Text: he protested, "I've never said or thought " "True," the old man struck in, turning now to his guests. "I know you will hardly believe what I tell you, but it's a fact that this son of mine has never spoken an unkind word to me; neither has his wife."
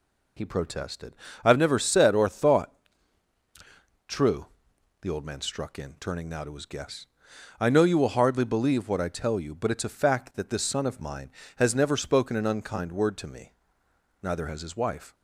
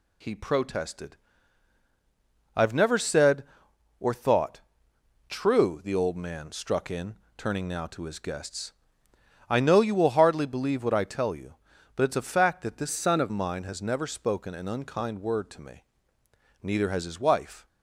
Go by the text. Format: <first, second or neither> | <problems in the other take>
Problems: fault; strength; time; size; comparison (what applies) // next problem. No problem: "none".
first | changes voice from "son" to "of"; from 12.9 to 13.3 s; 0.4 s long